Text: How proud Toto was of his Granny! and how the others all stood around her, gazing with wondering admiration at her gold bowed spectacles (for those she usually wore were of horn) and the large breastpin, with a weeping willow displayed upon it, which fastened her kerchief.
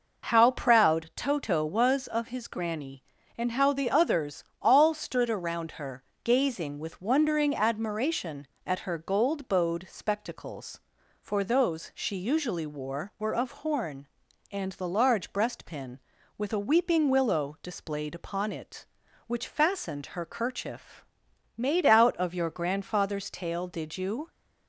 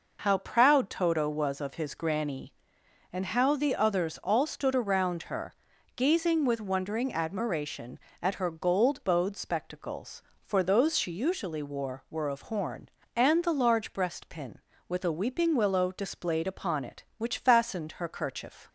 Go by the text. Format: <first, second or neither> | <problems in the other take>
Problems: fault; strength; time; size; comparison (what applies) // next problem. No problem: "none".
second | pauses between "others" and "all"; slight; at 4.4 s; 0.20 s long // goes on to say "Made out of your grandfather's tail did you"; strong; from 21.5 s on; 2.7 s long